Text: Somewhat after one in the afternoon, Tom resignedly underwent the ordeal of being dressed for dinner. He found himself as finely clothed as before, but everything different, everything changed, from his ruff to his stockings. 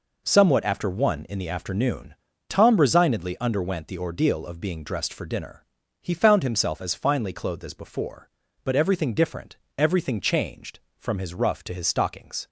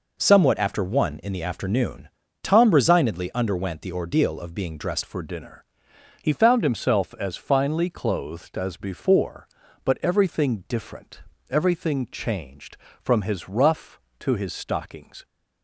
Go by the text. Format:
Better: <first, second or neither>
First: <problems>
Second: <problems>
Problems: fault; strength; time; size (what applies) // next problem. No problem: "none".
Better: first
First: none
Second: changes voice at "for"; from 5.0 s on; 10.2 s long